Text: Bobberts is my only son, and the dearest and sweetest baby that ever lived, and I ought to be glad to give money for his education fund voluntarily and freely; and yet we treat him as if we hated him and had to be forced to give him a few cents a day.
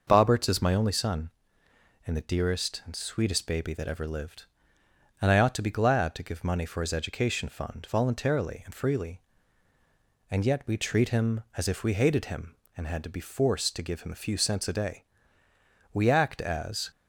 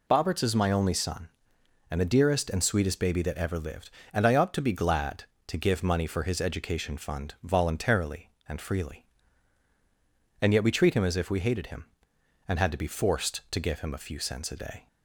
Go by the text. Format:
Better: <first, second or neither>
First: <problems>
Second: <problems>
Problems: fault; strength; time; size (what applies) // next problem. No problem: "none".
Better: second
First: goes on to say "We act as"; noticeable; from 15.9 s on; 0.98 s long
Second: none